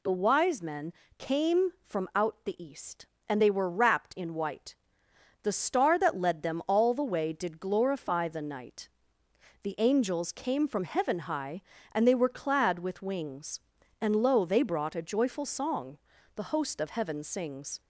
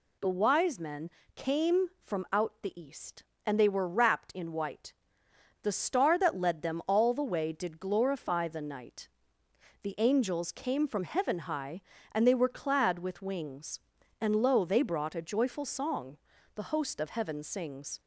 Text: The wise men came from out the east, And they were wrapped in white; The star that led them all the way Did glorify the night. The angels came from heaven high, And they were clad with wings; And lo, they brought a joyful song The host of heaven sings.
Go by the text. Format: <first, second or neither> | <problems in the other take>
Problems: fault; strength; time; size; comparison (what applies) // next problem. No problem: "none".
neither | pauses between "men" and "came"; slight; the same in both // pauses between "song" and "The"; the same in both